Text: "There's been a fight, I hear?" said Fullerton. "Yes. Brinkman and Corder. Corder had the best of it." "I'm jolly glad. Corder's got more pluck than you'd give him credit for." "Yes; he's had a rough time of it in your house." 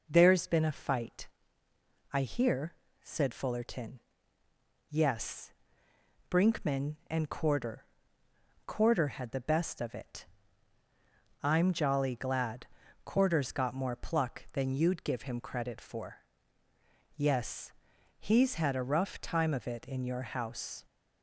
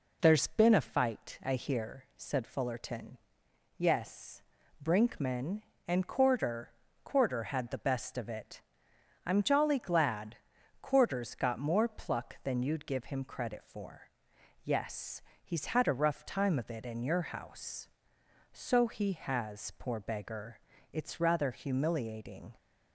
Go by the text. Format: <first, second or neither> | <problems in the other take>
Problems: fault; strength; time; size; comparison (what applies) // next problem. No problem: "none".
first | goes on to say "So he has poor beggar It's rather humiliating"; strong; from 18.5 s on; 4.0 s long